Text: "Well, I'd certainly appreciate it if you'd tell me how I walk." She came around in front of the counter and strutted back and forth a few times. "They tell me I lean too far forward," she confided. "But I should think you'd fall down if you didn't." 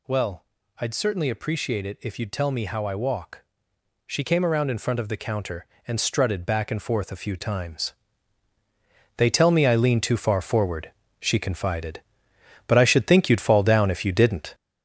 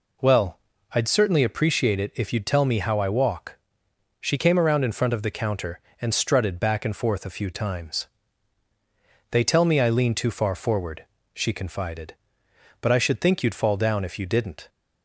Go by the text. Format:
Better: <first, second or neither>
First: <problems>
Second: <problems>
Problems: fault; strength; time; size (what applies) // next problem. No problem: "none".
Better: second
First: gets louder; throughout; 6.5 dB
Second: none